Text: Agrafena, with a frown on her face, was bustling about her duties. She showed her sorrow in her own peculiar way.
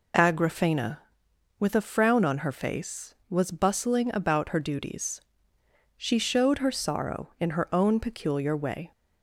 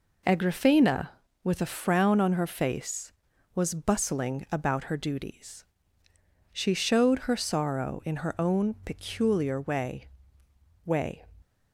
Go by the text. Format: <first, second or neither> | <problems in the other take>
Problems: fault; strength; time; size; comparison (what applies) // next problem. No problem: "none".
first | says "way" twice; at 10.8 s